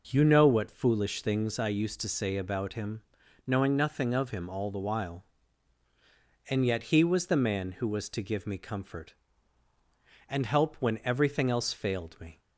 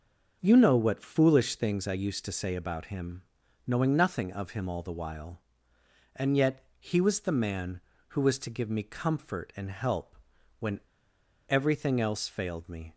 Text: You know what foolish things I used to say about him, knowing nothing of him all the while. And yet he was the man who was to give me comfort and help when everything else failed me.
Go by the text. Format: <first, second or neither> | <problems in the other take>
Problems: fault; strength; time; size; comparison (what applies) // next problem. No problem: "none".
first | starts louder than the rest; until 1.4 s; 6.5 dB // pauses between "yet" and "he"; slight; at 6.6 s; 0.16 s long // pauses between "help" and "when"; noticeable; at 10.1 s; 0.46 s long // pauses between "when" and "everything"; noticeable; at 10.7 s; 0.71 s long